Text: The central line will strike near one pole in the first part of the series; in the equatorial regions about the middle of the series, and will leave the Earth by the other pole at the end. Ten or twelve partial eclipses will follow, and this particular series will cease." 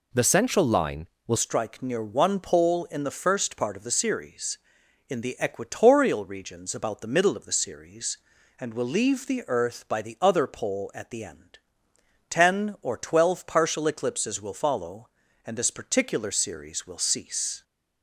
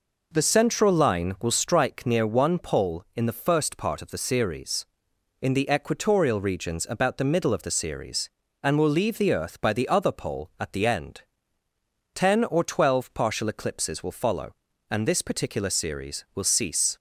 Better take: second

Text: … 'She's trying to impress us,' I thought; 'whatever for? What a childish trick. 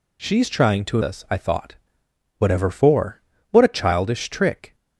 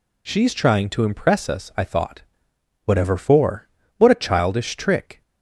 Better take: second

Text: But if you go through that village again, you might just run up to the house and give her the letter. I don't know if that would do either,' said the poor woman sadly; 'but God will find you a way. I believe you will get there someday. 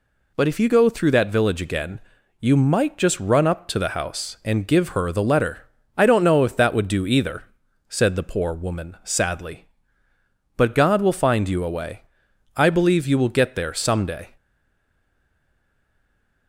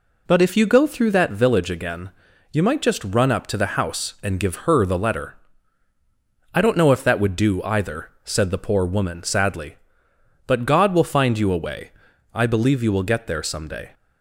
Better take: second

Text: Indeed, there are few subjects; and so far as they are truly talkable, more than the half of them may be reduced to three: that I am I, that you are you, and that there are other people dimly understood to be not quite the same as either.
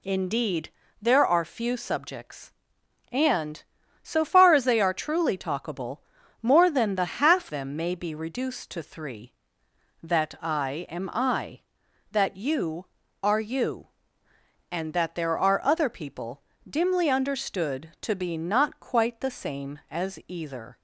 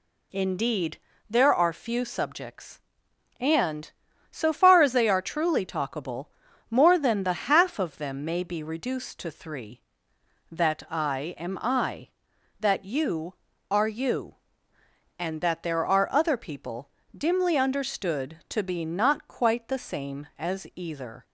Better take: second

